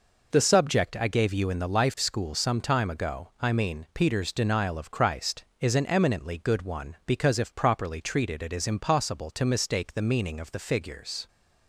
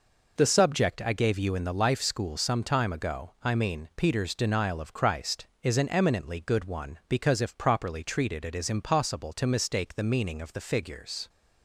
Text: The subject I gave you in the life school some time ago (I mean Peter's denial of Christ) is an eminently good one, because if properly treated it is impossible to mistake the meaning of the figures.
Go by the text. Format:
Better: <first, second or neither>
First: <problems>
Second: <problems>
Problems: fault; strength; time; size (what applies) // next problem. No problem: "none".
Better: neither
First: none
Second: none